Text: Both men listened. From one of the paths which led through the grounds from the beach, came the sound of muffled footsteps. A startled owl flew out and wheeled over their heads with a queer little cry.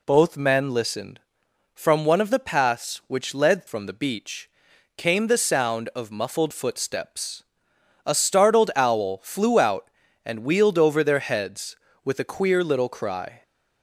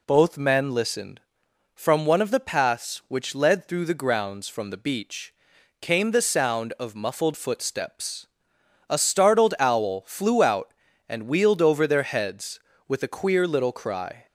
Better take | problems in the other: second | skips "through the grounds"; at 3.6 s

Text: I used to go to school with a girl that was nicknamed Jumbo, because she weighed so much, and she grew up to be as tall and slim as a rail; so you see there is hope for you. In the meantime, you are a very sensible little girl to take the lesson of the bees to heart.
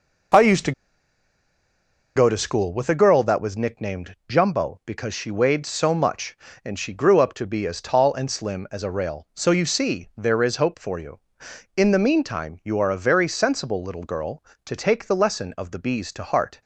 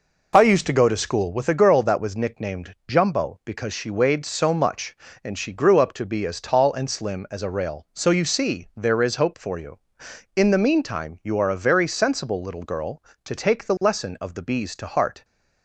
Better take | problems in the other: second | pauses between "to" and "go"; strong; at 0.7 s; 1.4 s long

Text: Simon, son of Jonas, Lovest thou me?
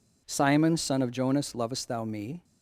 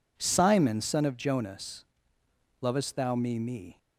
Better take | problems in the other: first | says "me" twice; at 3.3 s

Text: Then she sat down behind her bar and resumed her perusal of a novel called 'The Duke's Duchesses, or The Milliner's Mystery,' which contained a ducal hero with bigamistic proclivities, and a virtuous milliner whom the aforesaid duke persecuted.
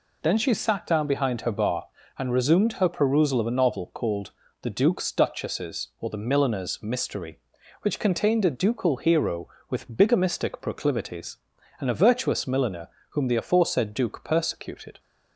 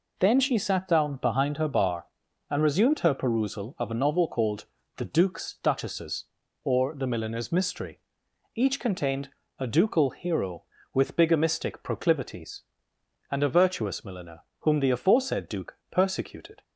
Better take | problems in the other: first | pauses between "called" and "The"; slight; at 4.6 s; 0.32 s long; slight in the first // says "each" for "which"; at 8.5 s // pauses between "contained" and "a"; slight; at 9.2 s; 0.30 s long // pauses between "milliner" and "whom"; slight; at 14.4 s; 0.18 s long; slight in the first

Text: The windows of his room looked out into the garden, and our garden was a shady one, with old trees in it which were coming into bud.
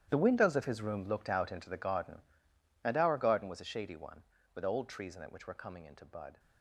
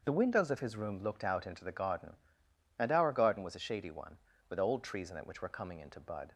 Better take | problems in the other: second | gets quieter; strong; throughout; 15.5 dB // starts louder than the rest; strong; until 1.1 s; 11 dB; also in the second

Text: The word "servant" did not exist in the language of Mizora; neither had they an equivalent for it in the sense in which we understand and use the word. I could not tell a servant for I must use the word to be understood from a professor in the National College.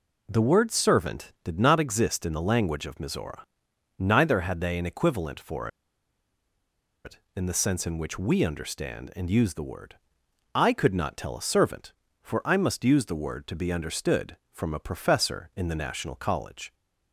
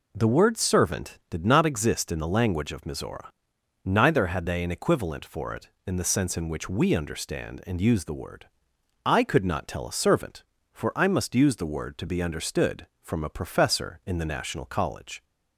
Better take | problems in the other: second | pauses between "for" and "it"; strong; at 5.6 s; 1.3 s long

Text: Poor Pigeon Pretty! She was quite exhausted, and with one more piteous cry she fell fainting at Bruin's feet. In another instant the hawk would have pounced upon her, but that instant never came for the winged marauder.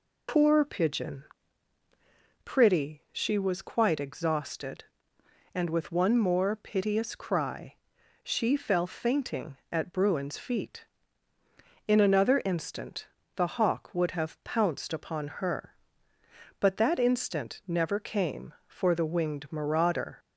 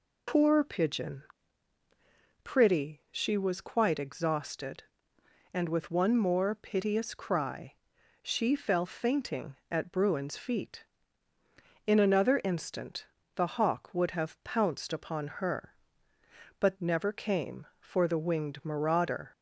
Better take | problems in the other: first | pauses between "Pigeon" and "Pretty"; at 1.2 s; 1.2 s long; also in the first // pauses between "cry" and "she"; noticeable; at 7.7 s; 0.48 s long; noticeable in the first // pauses between "instant" and "the"; slight; at 13.0 s; 0.30 s long; slight in the first // skips "that instant"; at 16.7 s

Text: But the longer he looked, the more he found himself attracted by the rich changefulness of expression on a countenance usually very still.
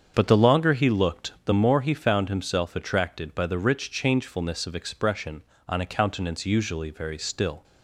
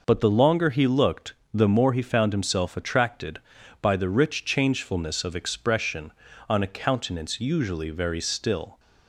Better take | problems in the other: second | starts louder than the rest; strong; until 1.4 s; 7.5 dB

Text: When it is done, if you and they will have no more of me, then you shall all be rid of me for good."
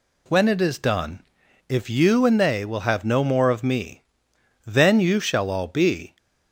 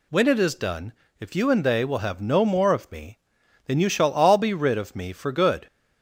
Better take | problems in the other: second | stops before "rid of me for good"; at 6.1 s

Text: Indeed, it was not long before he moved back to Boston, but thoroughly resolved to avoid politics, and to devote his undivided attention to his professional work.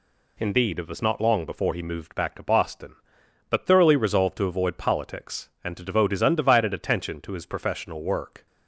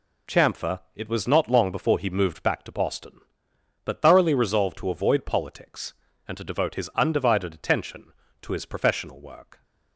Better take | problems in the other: first | says "Chamfer" for "Indeed"; at 0.2 s

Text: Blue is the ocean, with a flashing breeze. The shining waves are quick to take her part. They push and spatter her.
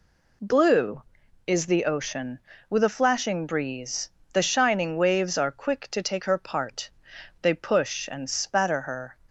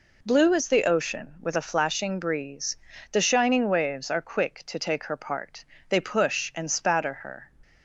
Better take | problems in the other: neither | none

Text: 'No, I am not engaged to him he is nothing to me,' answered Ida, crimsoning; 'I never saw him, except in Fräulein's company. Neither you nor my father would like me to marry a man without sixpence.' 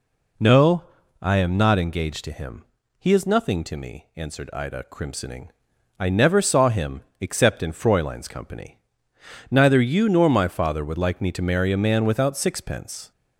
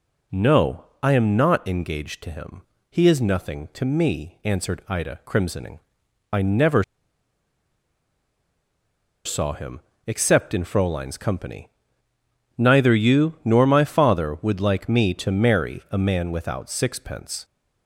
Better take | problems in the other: first | pauses between "him" and "he"; slight; at 2.6 s; 0.28 s long; slight in the first // pauses between "never" and "saw"; strong; at 6.8 s; 2.4 s long

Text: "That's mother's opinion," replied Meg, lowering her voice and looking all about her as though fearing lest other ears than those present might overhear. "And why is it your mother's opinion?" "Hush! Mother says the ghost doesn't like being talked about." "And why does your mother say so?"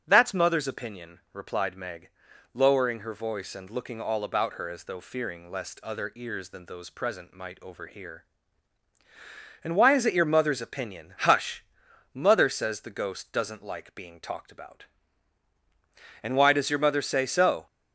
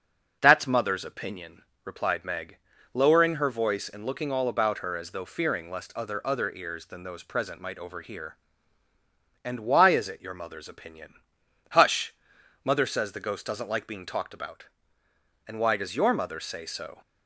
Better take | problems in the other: first | starts louder than the rest; noticeable; until 1.4 s; 6 dB; also in the first // says "other" twice; at 6.2 s

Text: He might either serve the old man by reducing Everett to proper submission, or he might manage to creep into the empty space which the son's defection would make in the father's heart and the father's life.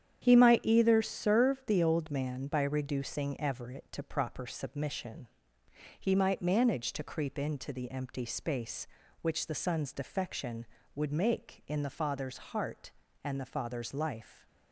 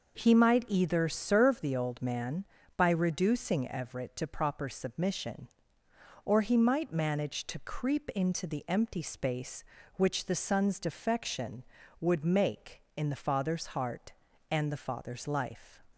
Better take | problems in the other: second | starts louder than the rest; strong; until 1.2 s; 9 dB // skips "or"; at 5.6 s

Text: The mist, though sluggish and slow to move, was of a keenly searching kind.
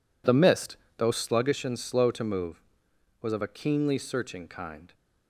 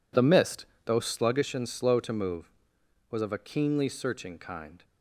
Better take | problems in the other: neither | none

